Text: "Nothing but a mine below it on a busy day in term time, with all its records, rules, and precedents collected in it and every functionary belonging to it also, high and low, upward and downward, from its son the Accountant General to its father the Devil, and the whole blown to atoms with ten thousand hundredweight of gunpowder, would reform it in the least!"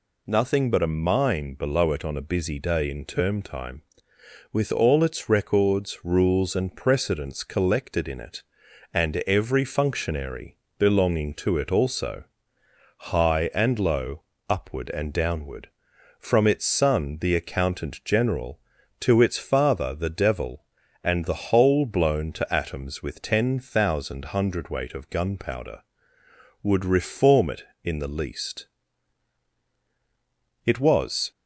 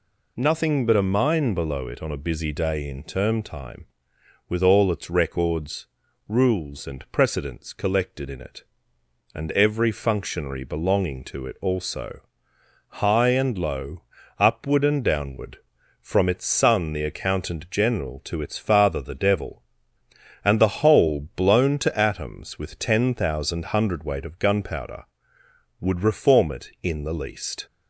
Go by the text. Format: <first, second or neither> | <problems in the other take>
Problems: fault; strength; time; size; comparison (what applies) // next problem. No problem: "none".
second | pauses between "functionary" and "belonging"; slight; at 10.5 s; 0.20 s long // goes on to say "It was"; noticeable; from 30.6 s on; 0.66 s long